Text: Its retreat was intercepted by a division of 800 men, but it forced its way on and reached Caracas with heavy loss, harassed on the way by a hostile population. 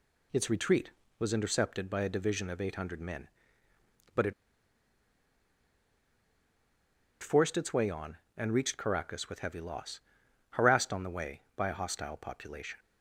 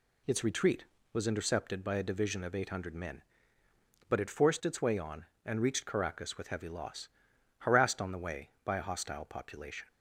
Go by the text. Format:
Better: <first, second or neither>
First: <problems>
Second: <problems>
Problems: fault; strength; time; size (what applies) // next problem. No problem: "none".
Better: second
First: pauses between "it" and "forced"; strong; at 4.3 s; 2.8 s long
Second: none